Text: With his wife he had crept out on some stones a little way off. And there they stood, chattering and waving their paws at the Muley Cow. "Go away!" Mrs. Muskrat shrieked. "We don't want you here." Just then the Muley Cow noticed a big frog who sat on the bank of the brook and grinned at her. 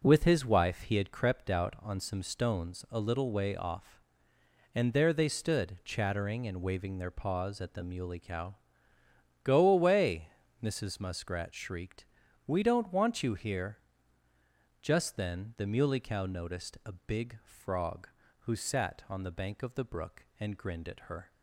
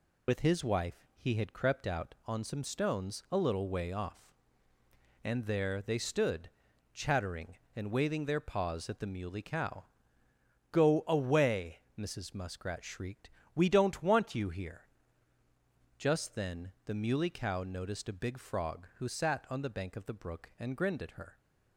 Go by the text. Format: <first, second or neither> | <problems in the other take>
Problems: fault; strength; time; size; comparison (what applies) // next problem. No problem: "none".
first | loses the start of "With"; at 0.2 s; 50 ms